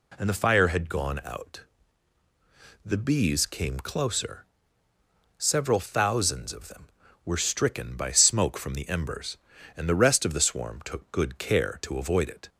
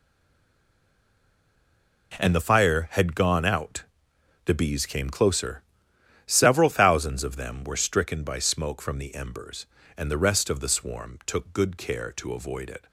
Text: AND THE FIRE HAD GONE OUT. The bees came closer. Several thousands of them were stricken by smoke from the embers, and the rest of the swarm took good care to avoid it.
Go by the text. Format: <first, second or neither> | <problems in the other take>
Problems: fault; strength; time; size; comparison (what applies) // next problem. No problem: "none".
first | stays silent before the first word; noticeable; until 2.1 s; 2.1 s long